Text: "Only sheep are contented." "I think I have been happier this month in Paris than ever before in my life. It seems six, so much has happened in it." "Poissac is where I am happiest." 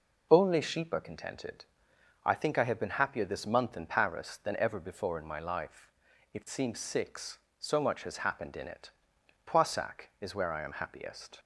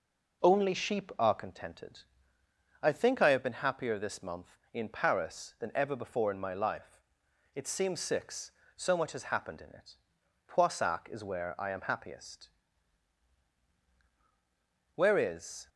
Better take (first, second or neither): first